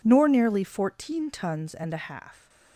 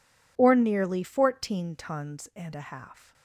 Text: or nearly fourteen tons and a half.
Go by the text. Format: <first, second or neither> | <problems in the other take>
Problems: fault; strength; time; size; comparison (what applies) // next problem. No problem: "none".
second | says "nor" for "or"; at 0.0 s